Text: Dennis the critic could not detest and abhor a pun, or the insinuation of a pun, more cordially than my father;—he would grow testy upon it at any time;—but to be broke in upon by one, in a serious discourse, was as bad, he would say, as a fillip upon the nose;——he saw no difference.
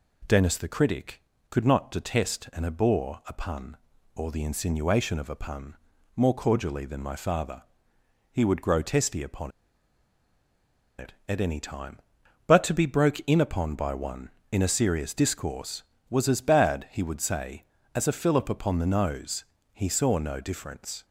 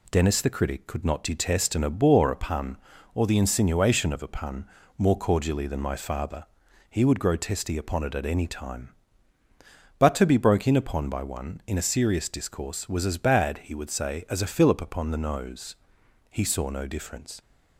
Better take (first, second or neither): second